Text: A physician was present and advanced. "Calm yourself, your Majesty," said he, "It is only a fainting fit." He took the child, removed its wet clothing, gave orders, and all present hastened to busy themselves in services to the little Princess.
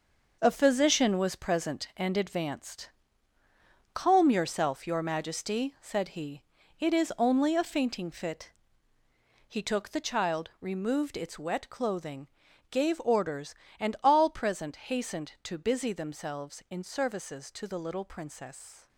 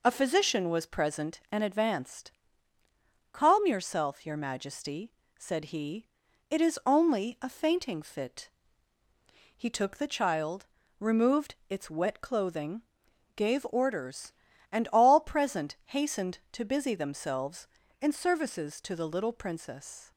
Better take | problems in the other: second | gets quieter; strong; throughout; 8.5 dB

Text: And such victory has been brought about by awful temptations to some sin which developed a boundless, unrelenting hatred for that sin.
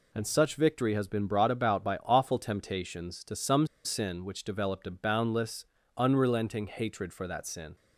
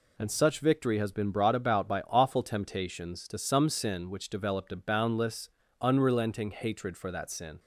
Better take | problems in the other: second | pauses between "some" and "sin"; slight; at 3.6 s; 0.18 s long

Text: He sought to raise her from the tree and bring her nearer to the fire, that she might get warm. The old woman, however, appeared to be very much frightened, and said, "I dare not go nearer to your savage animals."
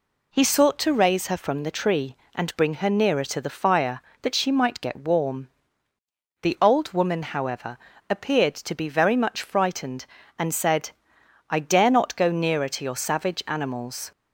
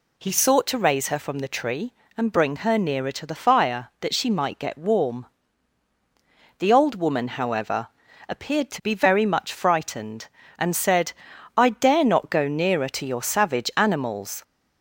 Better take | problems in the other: neither | none

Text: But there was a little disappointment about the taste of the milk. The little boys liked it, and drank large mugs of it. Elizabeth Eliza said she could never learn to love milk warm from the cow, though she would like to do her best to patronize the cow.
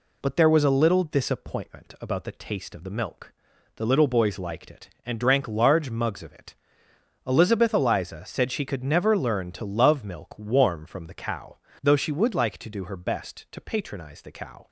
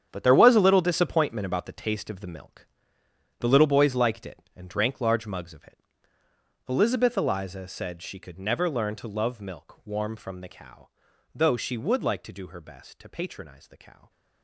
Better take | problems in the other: first | gets quieter; strong; throughout; 13 dB

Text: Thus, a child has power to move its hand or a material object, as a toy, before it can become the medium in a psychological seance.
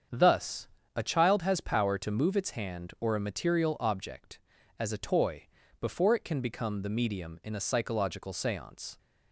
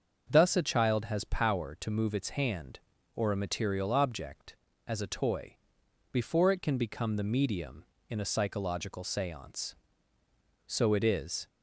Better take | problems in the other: first | starts louder than the rest; until 1.2 s; 6.5 dB; strong in the first // goes on to say "So it is"; noticeable; from 10.6 s on; 0.80 s long

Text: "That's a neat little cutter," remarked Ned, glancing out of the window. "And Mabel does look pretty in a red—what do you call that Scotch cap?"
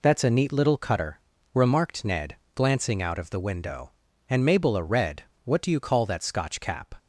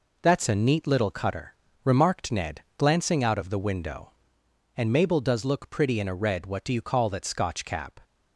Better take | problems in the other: second | skips "does look pretty in"; at 4.7 s

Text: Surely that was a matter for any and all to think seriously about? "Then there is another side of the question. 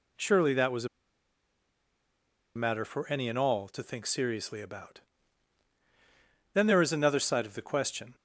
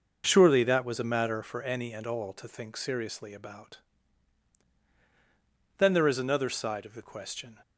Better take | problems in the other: second | pauses between "a" and "matter"; strong; at 0.8 s; 1.6 s long

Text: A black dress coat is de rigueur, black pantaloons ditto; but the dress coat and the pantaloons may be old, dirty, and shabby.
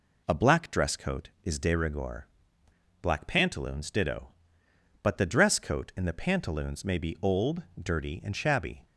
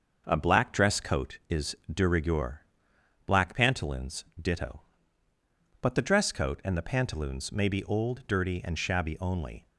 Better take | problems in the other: first | starts louder than the rest; until 1.2 s; 6.5 dB // pauses between "is" and "de"; slight; at 1.7 s; 0.16 s long // pauses between "pantaloons" and "ditto"; slight; at 4.2 s; 0.16 s long // goes on to say "Only"; slight; from 9.1 s on; 0.46 s long

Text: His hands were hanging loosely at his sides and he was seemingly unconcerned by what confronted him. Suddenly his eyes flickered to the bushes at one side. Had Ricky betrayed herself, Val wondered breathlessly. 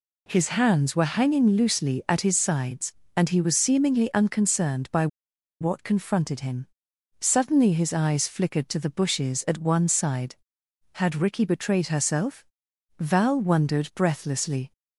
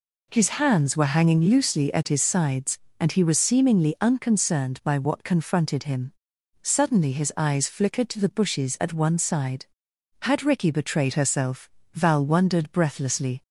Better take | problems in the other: second | pauses between "by" and "what"; noticeable; at 5.0 s; 0.53 s long

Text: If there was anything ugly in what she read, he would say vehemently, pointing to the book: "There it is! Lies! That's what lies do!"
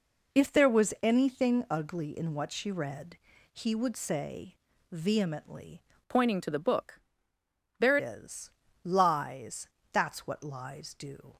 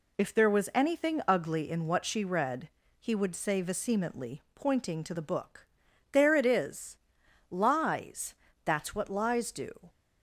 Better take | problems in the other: second | pauses between "say" and "vehemently"; slight; at 4.5 s; 0.36 s long // changes voice from "pointing" to "it"; from 6.0 to 8.0 s; 2.0 s long

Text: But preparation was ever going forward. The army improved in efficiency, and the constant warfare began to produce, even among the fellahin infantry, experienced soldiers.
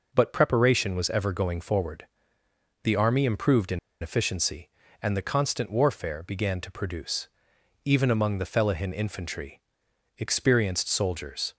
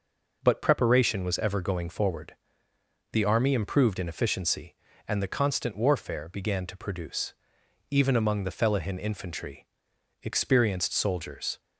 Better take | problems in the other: second | pauses between "in" and "efficiency"; slight; at 3.7 s; 0.24 s long

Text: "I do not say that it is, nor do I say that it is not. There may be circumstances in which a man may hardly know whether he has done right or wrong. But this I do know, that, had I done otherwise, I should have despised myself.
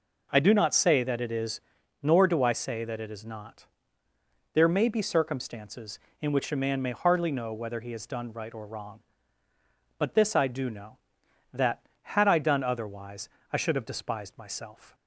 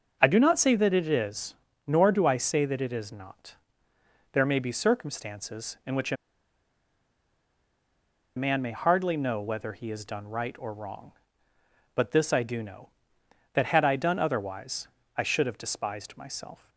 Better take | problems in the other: first | starts louder than the rest; noticeable; until 1.2 s; 6 dB // pauses between "a" and "man"; strong; at 6.1 s; 2.2 s long

